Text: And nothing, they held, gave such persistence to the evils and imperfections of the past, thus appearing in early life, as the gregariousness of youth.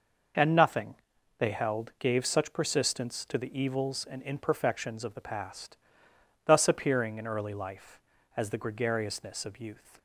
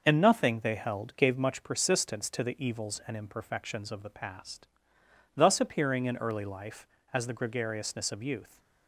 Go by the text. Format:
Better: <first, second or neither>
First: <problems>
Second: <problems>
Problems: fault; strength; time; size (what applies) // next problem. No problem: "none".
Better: first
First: none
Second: says "much" for "such"; at 1.3 s